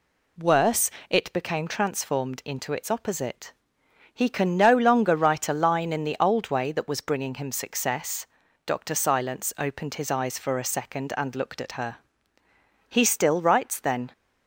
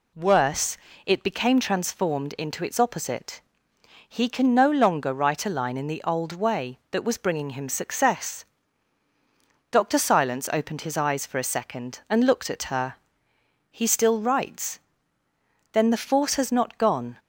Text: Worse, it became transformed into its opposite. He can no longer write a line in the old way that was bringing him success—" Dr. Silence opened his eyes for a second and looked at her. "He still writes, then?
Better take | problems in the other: first | goes on to say "The force has not gone"; noticeable; from 15.8 s on; 1.2 s long

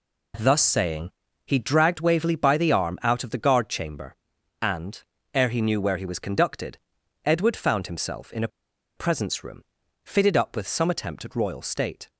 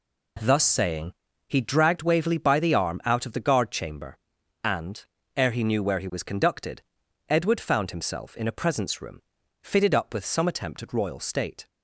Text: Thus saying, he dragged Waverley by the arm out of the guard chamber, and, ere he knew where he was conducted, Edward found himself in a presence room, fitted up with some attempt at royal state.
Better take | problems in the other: second | pauses between "a" and "presence"; noticeable; at 8.4 s; 0.49 s long

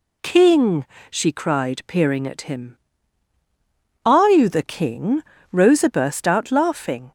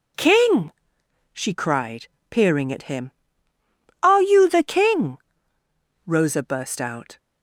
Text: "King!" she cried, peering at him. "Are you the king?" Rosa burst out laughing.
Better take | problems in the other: first | stops before "laughing"; at 7.1 s

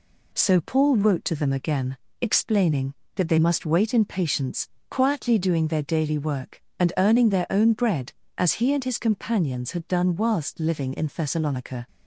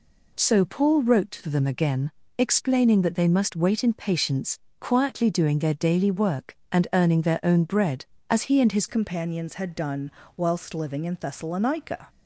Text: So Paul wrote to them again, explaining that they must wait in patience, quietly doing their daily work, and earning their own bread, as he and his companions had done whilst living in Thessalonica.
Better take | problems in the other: first | changes voice at "companions"; from 8.8 s on; 3.2 s long // pauses between "done" and "whilst"; slight; at 10.1 s; 0.26 s long

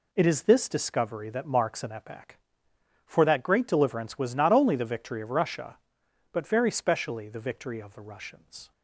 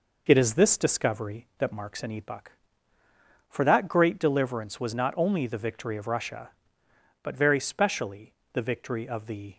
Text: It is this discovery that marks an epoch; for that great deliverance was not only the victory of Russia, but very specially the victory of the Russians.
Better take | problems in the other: first | pauses between "specially" and "the"; slight; at 8.3 s; 0.18 s long // stops before "Russians"; at 9.5 s

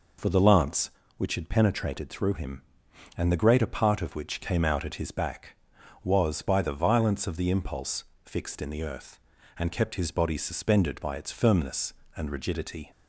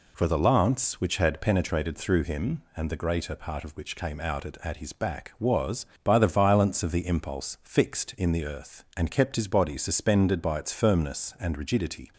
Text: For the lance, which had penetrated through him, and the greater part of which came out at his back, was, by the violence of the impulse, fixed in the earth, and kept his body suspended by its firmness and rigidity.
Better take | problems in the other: first | says "at" twice; at 4.6 s

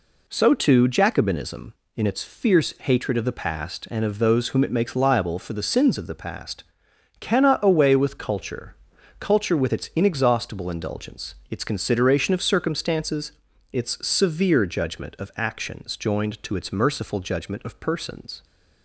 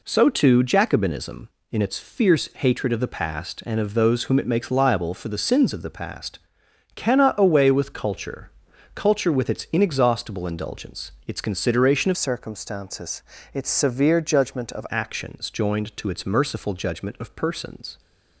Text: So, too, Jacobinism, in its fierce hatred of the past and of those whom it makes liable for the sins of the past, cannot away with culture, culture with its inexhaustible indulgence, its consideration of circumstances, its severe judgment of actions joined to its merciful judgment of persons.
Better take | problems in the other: first | changes voice from "circumstances" to "of"; from 12.1 to 14.8 s; 2.7 s long

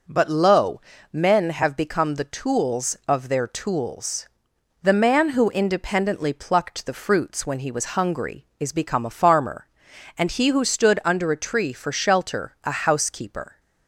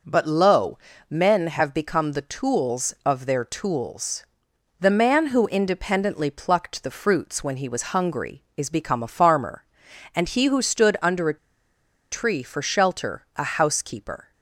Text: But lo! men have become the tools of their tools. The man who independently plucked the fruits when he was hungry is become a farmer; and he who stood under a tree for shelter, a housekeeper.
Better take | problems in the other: first | pauses between "a" and "tree"; noticeable; at 11.3 s; 0.74 s long

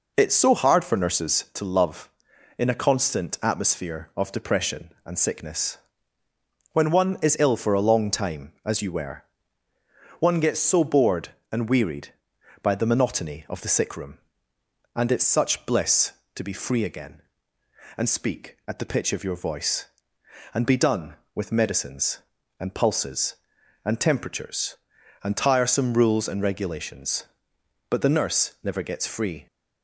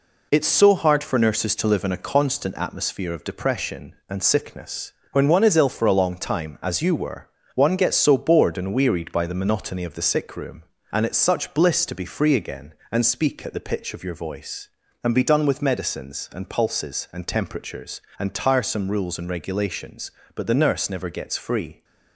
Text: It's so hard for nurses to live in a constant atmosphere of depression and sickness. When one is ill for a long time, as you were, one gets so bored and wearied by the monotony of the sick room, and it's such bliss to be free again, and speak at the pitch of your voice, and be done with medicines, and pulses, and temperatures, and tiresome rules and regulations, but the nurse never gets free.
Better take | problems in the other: second | says "love" for "live"; at 1.6 s

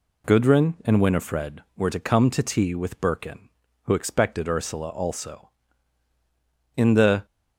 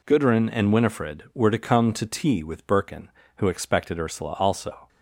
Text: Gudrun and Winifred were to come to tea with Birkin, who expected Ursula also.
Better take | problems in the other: second | goes on to say "In the"; from 6.7 s on; 0.50 s long

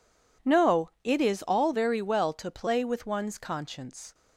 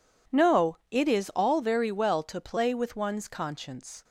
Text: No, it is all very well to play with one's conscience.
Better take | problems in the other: neither | none

